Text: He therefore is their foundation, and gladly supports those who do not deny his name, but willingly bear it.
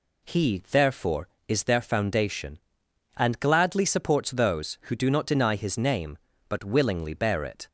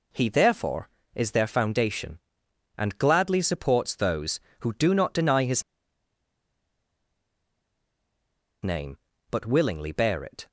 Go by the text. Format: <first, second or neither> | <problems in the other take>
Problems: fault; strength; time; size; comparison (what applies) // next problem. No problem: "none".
first | pauses between "his" and "name"; strong; at 5.6 s; 3.0 s long